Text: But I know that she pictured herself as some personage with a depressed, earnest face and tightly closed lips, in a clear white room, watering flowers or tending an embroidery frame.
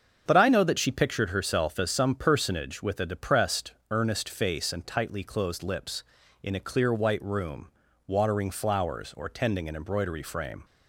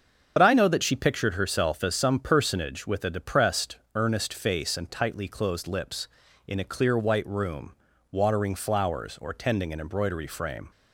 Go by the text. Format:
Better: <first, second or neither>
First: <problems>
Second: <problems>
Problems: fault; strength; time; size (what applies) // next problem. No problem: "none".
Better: first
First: starts louder than the rest; until 1.2 s; 7 dB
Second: loses the start of "But"; at 0.3 s; 45 ms // starts louder than the rest; until 1.3 s; 6.5 dB